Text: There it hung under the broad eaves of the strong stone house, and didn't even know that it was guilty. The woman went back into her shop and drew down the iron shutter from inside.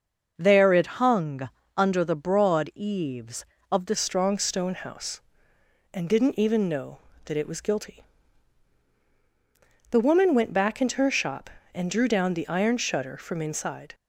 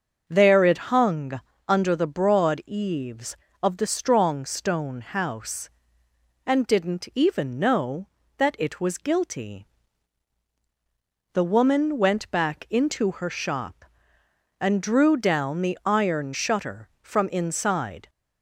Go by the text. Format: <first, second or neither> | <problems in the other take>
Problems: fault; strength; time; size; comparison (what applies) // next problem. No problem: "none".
second | starts louder than the rest; until 1.3 s; 6 dB; also in the second // pauses between "hung" and "under"; slight; at 1.4 s; 0.28 s long; slight in the second // changes voice at "strong"; from 3.9 s on; 10.0 s long